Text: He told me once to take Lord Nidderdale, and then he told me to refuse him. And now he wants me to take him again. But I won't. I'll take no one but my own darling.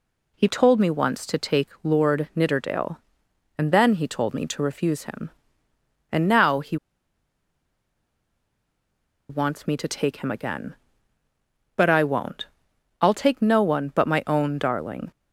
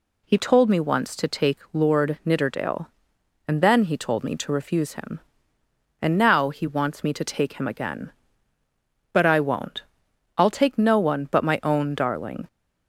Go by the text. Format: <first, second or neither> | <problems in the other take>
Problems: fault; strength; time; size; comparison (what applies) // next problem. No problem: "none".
second | pauses between "take" and "Lord"; slight; at 1.6 s; 0.16 s long; slight in the second // pauses between "he" and "wants"; strong; at 6.7 s; 2.5 s long